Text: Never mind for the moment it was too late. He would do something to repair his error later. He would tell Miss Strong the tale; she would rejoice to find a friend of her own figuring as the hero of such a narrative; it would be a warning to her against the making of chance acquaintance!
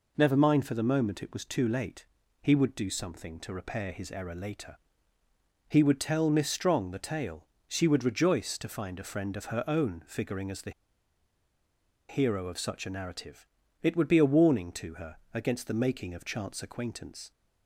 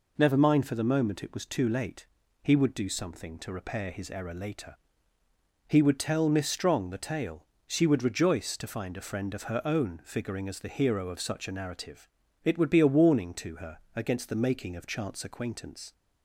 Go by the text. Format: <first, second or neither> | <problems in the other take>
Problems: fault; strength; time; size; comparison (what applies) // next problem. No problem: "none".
second | pauses between "the" and "hero"; strong; at 10.7 s; 1.3 s long // pauses between "her" and "against"; slight; at 15.1 s; 0.16 s long; slight in the second